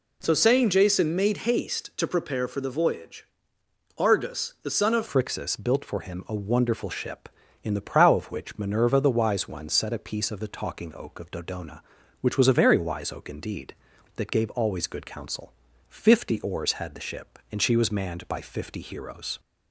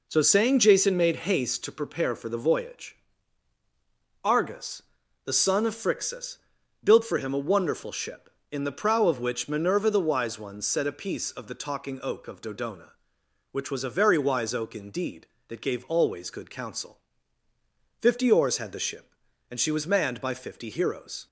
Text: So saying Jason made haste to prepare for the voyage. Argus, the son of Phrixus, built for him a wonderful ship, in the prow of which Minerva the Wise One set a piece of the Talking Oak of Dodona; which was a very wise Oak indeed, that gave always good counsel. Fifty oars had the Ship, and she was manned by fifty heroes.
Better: second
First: changes voice at "Phrixus"; from 5.0 s on; 14.3 s long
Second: none

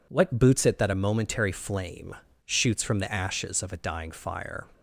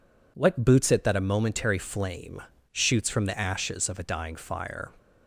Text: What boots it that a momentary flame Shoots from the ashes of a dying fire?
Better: neither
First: pauses between "flame" and "Shoots"; slight; at 2.1 s; 0.32 s long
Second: pauses between "flame" and "Shoots"; slight; at 2.4 s; 0.32 s long

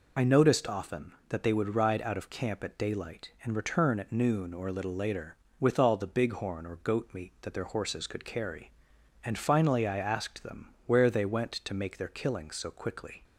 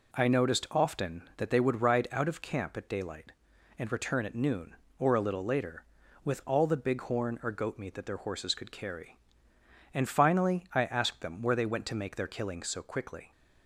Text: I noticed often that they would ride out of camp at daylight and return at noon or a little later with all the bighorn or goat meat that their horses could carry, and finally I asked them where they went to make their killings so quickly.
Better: second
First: loses the start of "I"; at 0.1 s; 20 ms // pauses between "them" and "where"; slight; at 10.6 s; 0.18 s long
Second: none

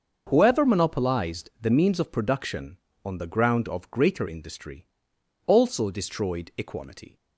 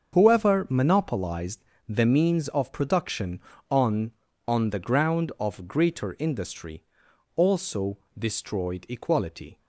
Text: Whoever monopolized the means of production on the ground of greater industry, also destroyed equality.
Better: first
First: starts louder than the rest; until 1.3 s; 6.5 dB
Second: starts louder than the rest; until 1.1 s; 6.5 dB // pauses between "monopolized" and "the"; slight; at 1.6 s; 0.24 s long // says "on" twice; at 4.4 s // pauses between "also" and "destroyed"; slight; at 7.9 s; 0.18 s long

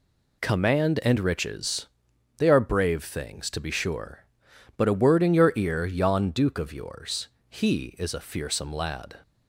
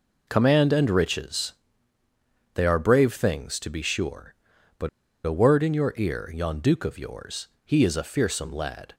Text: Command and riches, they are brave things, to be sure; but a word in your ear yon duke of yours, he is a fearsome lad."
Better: first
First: none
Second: pauses between "but" and "a"; at 4.8 s; 0.37 s long

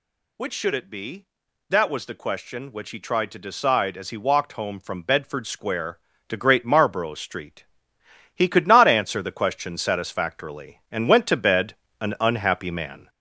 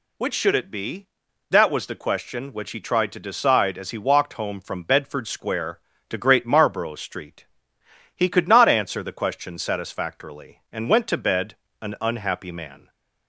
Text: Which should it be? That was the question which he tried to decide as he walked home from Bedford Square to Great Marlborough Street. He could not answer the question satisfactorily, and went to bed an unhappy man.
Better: second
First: gets louder; noticeable; throughout; 4.5 dB // pauses between "bed" and "an"; slight; at 11.7 s; 0.26 s long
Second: pauses between "bed" and "an"; slight; at 11.5 s; 0.26 s long

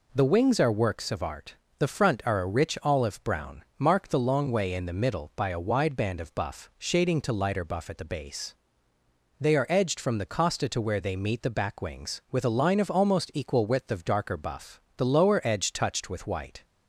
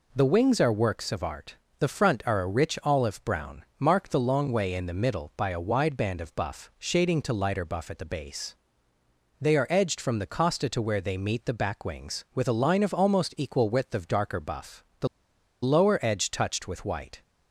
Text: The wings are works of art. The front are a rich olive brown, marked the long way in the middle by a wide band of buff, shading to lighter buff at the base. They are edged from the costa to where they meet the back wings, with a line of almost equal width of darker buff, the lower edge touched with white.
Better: first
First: none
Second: pauses between "the" and "lower"; noticeable; at 15.0 s; 0.55 s long

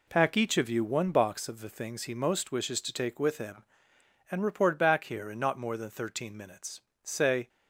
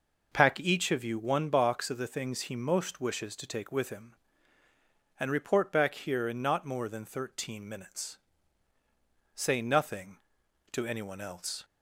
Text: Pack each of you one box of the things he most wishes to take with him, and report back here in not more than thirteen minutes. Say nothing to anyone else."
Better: second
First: stops before "nothing to anyone else"; at 7.4 s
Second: none

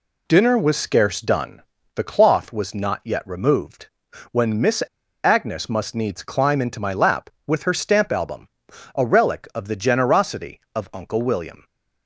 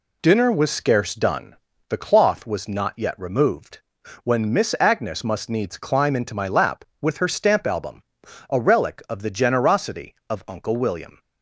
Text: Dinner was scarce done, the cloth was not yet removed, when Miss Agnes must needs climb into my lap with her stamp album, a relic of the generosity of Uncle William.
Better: second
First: pauses between "Miss" and "Agnes"; at 4.8 s; 0.42 s long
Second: none

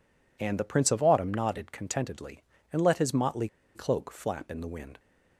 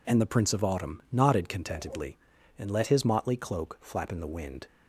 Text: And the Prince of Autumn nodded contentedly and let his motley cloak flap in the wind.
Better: second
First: pauses between "motley" and "cloak"; slight; at 3.4 s; 0.27 s long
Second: none

